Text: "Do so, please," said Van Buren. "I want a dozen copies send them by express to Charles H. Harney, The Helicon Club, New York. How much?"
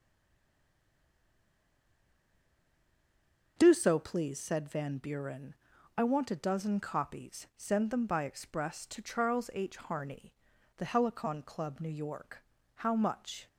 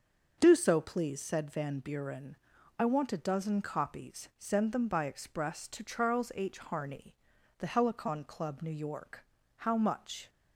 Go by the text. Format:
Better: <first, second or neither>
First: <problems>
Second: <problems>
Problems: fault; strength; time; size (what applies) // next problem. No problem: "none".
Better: second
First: stays silent before the first word; strong; until 3.5 s; 3.5 s long // starts louder than the rest; until 4.5 s; 6.5 dB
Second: starts louder than the rest; until 1.3 s; 6.5 dB